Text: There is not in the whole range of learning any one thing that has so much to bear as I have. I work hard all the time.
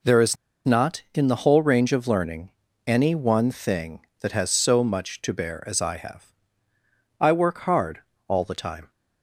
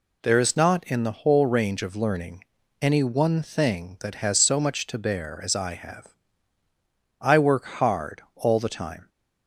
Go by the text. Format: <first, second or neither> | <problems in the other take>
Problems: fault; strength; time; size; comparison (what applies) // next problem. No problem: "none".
second | pauses between "is" and "not"; slight; at 0.3 s; 0.29 s long // pauses between "learning" and "any"; slight; at 2.5 s; 0.36 s long; also in the second // pauses between "hard" and "all"; slight; at 7.9 s; 0.30 s long